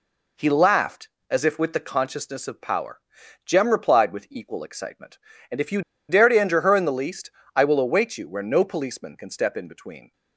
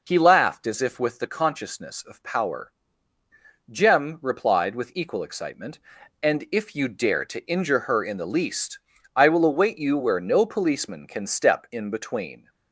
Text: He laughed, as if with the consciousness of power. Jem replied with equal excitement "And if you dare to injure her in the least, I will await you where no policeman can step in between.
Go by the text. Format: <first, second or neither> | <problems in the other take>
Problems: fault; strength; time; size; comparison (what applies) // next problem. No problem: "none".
second | pauses between "you" and "dare"; slight; at 5.8 s; 0.28 s long